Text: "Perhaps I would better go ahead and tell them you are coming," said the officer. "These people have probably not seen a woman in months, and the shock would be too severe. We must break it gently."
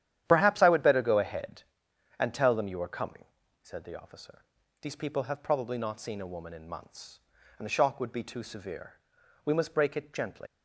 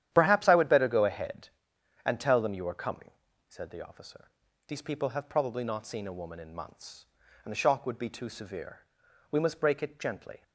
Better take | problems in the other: second | starts louder than the rest; strong; until 1.2 s; 11 dB; strong in the second // leaves "gently" unfinished; at 10.4 s; 100 ms

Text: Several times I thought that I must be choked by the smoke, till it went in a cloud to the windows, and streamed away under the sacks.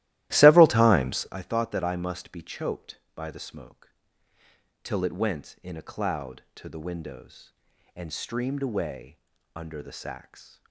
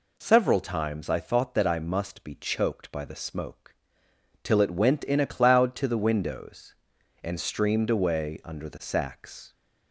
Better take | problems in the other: second | starts louder than the rest; strong; until 1.4 s; 15.5 dB // pauses between "away" and "under"; at 9.1 s; 0.38 s long

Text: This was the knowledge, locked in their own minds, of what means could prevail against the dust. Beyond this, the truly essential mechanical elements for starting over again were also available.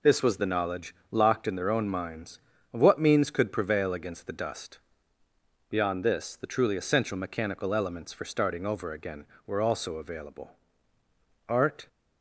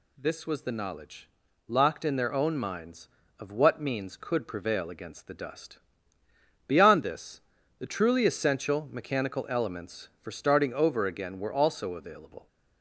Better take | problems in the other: second | goes on to say "Art"; slight; from 11.4 s on; 0.40 s long

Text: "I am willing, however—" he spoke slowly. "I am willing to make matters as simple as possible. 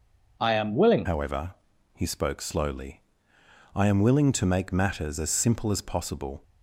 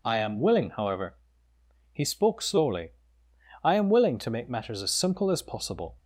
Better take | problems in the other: second | changes voice at "however"; from 1.0 s on; 5.4 s long

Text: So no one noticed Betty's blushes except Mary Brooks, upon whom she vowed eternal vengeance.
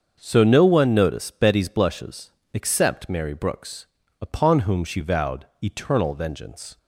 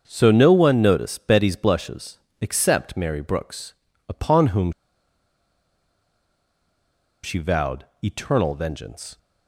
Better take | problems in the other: first | starts louder than the rest; until 1.0 s; 6.5 dB; also in the first // pauses between "blushes" and "except"; slight; at 2.1 s; 0.20 s long; slight in the first // pauses between "whom" and "she"; strong; at 4.7 s; 2.5 s long // pauses between "vowed" and "eternal"; slight; at 7.8 s; 0.18 s long; slight in the first

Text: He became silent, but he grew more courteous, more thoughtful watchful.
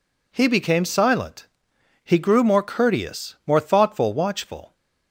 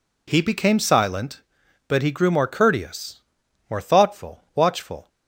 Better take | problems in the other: second | skips "but"; at 1.7 s

